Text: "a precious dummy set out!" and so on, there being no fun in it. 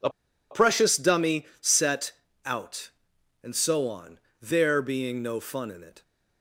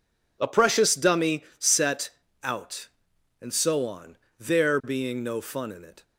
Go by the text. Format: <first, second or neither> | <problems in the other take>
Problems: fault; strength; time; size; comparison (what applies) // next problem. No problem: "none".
second | pauses between "a" and "precious"; at 0.0 s; 0.42 s long // pauses between "dummy" and "set"; slight; at 1.4 s; 0.16 s long; slight in the second // pauses between "set" and "out"; slight; at 2.1 s; 0.34 s long; slight in the second